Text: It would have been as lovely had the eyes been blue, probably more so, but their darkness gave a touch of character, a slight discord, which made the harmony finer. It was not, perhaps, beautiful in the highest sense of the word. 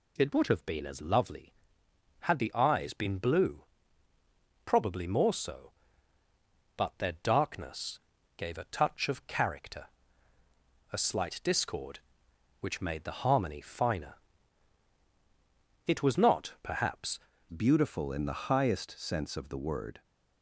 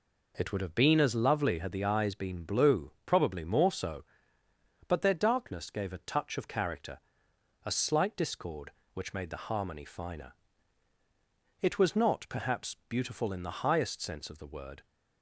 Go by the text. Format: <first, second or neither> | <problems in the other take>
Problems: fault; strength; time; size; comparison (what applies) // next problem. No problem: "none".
second | pauses between "darkness" and "gave"; at 7.9 s; 0.38 s long // changes voice at "beautiful"; from 17.4 s on; 2.6 s long